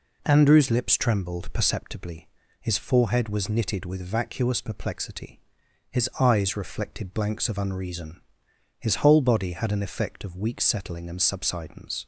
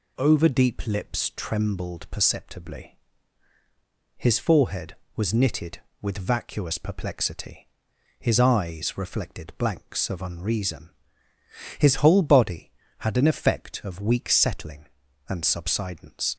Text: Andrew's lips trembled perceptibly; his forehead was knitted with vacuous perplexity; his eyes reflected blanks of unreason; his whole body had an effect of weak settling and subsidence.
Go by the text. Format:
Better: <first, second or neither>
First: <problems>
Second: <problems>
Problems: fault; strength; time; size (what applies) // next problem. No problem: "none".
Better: first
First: none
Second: says "Overdeep" for "Andrew's"; at 0.1 s